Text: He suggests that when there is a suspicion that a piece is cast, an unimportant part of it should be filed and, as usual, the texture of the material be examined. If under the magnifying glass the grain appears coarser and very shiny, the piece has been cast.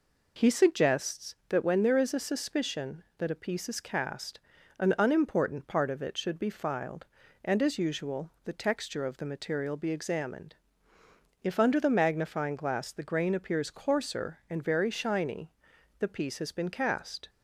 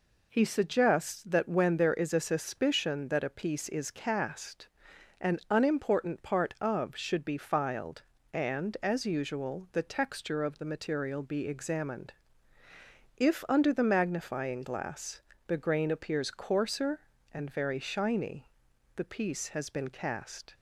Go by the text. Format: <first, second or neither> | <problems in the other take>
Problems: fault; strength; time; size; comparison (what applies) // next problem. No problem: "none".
first | skips "it"; at 6.9 s // pauses between "glass" and "the"; slight; at 15.2 s; 0.26 s long